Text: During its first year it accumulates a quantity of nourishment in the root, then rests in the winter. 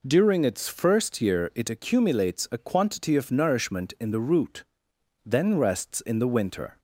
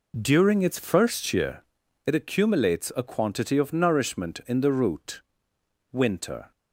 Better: first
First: none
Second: pauses between "year" and "it"; at 1.6 s; 0.42 s long // skips "then rests in the"; at 5.5 s

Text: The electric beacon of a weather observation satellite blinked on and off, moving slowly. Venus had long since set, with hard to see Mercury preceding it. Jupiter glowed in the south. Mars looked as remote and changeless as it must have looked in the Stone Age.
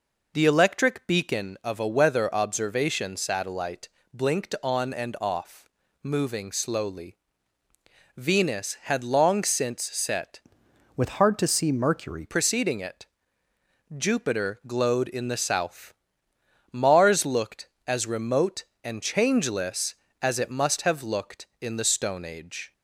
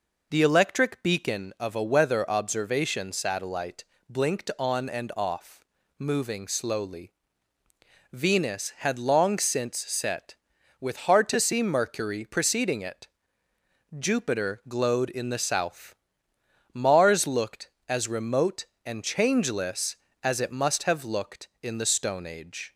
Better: second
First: pauses between "satellite" and "blinked"; slight; at 3.8 s; 0.24 s long // changes voice from "with" to "Mercury"; from 10.9 to 12.2 s; 1.3 s long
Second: pauses between "satellite" and "blinked"; slight; at 3.8 s; 0.24 s long

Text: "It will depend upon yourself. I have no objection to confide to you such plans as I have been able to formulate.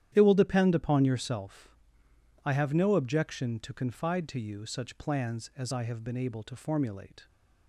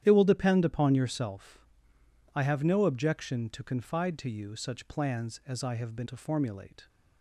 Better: first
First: starts louder than the rest; strong; until 1.1 s; 11 dB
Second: starts louder than the rest; strong; until 1.0 s; 10.5 dB // skips "able"; at 6.0 s

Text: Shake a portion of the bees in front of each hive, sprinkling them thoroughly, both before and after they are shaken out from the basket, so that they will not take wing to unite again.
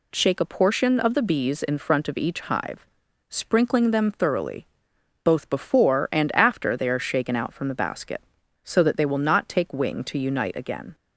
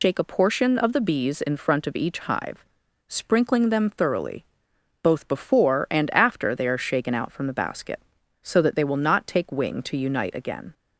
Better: first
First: none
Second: loses the start of "Shake"; at 0.0 s; 100 ms

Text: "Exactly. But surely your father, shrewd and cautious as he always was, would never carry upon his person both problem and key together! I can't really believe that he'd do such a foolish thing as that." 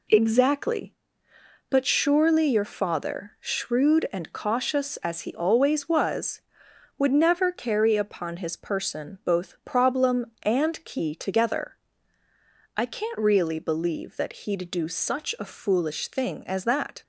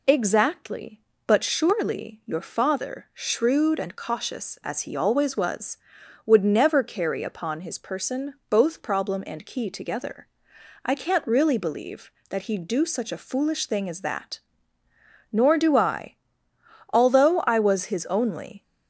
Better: first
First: none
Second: pauses between "person" and "both"; slight; at 8.3 s; 0.16 s long // goes on to say "Nor do I Although I was his only"; strong; from 15.3 s on; 3.3 s long

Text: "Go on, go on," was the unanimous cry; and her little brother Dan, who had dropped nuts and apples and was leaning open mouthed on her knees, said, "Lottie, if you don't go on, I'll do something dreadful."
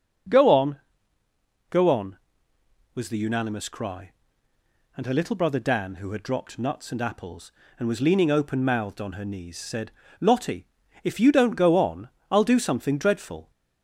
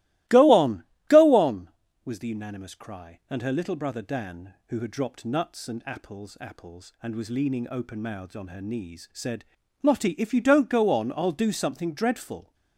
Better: first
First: starts louder than the rest; until 2.9 s; 6.5 dB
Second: starts louder than the rest; strong; until 1.5 s; 18 dB // says "apples" twice; at 6.3 s

